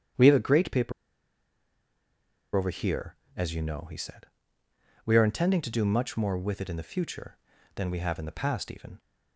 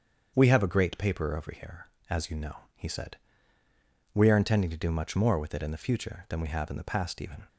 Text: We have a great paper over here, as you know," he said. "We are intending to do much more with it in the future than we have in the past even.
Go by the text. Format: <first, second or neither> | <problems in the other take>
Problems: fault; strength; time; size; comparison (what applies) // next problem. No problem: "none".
second | starts louder than the rest; strong; until 2.8 s; 9 dB; strong in the second // pauses between "paper" and "over"; strong; at 0.9 s; 1.6 s long